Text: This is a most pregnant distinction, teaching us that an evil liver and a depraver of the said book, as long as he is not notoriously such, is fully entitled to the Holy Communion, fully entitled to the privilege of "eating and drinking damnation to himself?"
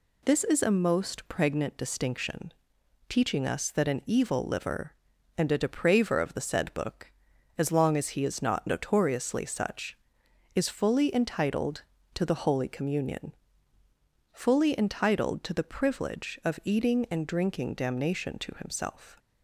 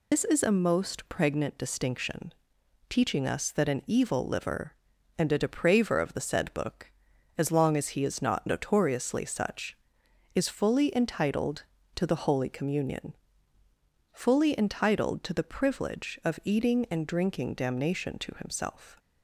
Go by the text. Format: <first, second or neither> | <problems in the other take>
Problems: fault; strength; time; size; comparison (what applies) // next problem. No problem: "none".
first | loses the start of "This"; at 0.1 s; 75 ms